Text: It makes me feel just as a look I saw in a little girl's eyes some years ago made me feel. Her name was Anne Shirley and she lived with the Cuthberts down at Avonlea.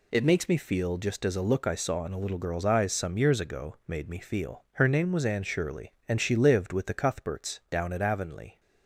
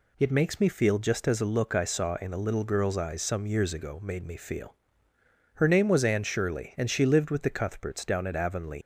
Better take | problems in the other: first | leaves "Avonlea" unfinished; at 8.8 s; 130 ms

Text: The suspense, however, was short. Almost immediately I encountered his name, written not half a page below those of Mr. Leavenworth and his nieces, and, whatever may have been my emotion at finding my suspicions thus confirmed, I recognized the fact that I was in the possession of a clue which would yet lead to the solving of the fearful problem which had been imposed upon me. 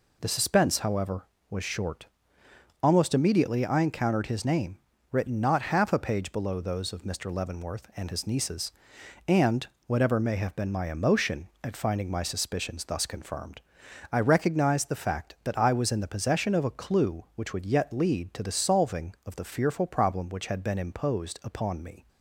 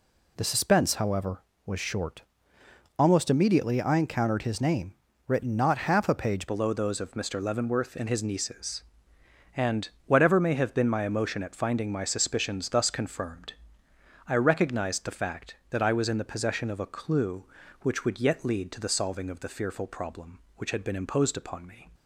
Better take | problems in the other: first | changes voice at "below"; from 6.4 s on; 15.4 s long

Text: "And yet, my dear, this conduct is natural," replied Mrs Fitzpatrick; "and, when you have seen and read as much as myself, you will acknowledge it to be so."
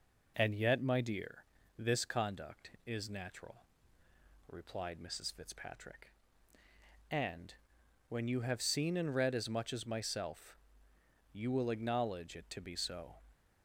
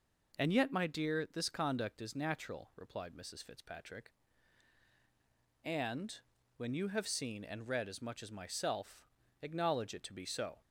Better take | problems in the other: first | skips "you will"; at 9.2 s

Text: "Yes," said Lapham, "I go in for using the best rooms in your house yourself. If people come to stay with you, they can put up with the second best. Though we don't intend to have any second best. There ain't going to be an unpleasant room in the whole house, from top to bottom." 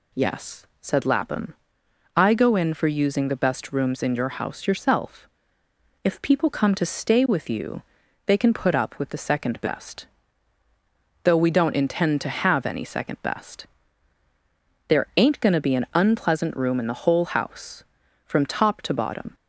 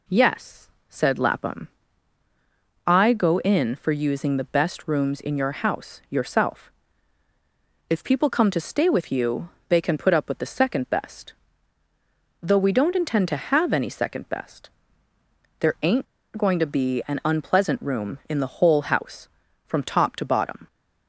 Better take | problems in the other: first | pauses between "ain't" and "going"; slight; at 16.0 s; 0.31 s long

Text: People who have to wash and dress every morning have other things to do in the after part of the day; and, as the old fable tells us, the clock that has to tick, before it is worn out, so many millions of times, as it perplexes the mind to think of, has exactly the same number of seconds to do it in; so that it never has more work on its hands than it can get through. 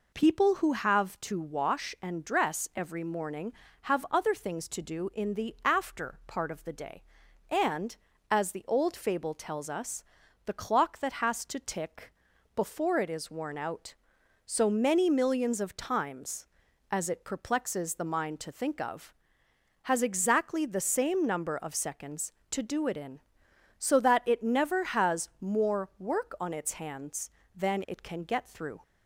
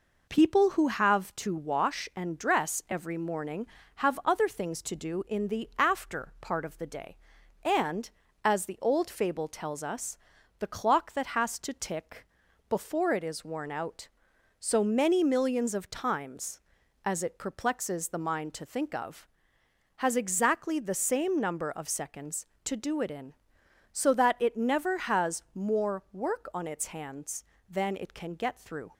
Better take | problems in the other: first | gets quieter; slight; throughout; 3 dB

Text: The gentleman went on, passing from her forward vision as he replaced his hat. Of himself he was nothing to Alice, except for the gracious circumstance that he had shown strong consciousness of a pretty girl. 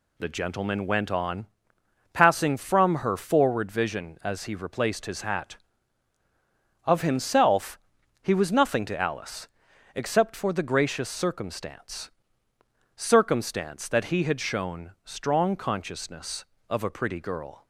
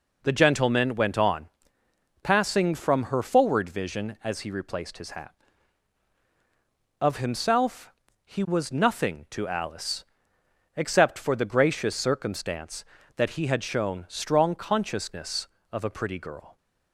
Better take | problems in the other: second | pauses between "himself" and "he"; at 7.7 s; 0.42 s long; slight in the second // says "circumstance" twice; at 12.9 s

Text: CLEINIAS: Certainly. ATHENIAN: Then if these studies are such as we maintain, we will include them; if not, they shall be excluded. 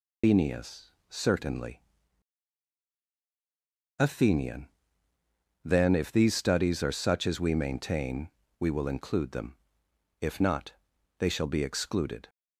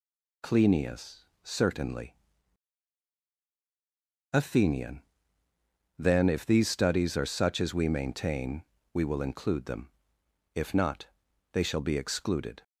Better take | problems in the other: second | loses the start of "CLEINIAS"; at 0.2 s; 165 ms

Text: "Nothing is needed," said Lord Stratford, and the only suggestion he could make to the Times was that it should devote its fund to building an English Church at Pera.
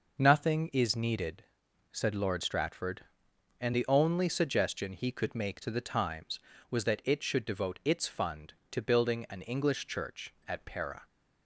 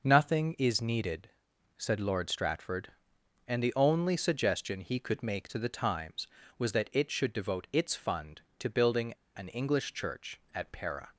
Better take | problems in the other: first | pauses between "building" and "an"; slight; at 9.1 s; 0.24 s long

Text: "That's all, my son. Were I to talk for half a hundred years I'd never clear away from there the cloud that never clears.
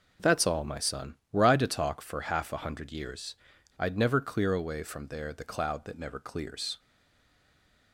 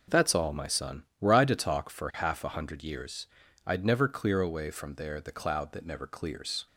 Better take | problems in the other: second | pauses between "years" and "I'd"; at 3.3 s; 0.42 s long; also in the second // stays silent after the last word; from 6.7 s on; 1.2 s long

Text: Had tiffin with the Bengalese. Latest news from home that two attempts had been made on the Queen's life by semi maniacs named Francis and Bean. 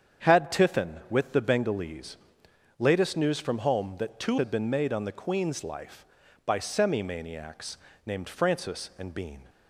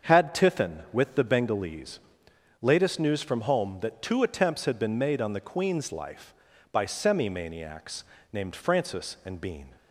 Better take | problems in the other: second | starts louder than the rest; strong; until 1.3 s; 8 dB; also in the second // skips "attempts"; at 4.3 s // pauses between "maniacs" and "named"; slight; at 7.7 s; 0.30 s long; slight in the second

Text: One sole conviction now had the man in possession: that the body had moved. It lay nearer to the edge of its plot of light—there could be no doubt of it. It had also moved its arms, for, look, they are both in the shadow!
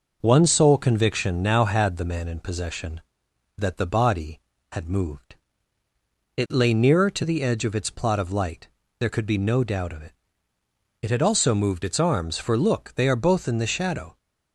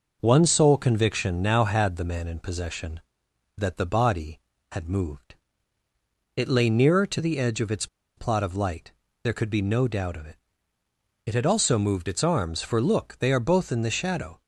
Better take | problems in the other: first | pauses between "its" and "plot"; slight; at 7.8 s; 0.29 s long

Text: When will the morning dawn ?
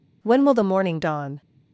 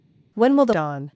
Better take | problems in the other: first | skips "morning"; at 0.7 s

